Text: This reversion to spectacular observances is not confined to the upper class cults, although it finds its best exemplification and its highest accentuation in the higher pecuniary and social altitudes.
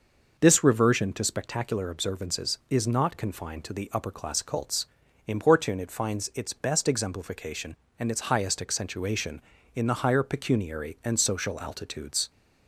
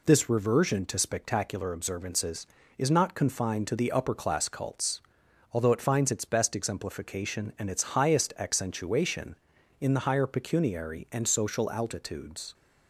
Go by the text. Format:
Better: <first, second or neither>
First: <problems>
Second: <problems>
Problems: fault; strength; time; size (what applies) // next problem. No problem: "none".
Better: second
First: says "importune" for "although"; at 5.2 s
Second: none